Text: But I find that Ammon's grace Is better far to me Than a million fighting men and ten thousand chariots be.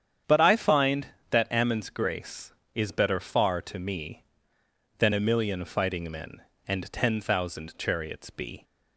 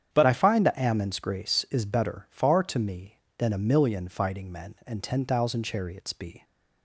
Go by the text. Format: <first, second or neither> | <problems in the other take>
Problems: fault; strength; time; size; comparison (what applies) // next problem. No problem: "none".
first | starts louder than the rest; strong; until 1.1 s; 8.5 dB; strong in the first // changes voice at "I"; from 0.2 s on; 6.2 s long